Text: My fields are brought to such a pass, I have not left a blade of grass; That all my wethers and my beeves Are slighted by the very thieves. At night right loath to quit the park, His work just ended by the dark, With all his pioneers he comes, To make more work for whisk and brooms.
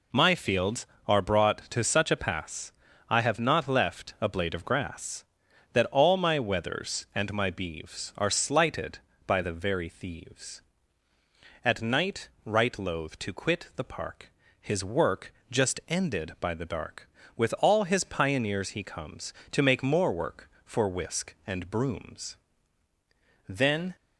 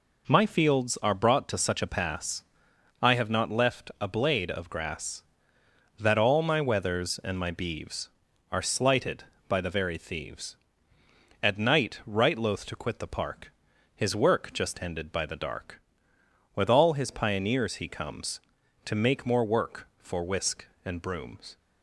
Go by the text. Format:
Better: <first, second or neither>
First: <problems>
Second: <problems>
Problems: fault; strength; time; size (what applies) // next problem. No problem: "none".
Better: second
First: pauses between "night" and "right"; slight; at 12.2 s; 0.16 s long // pauses between "work" and "just"; slight; at 15.3 s; 0.16 s long // goes on to say "Then"; slight; from 23.4 s on; 0.46 s long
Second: none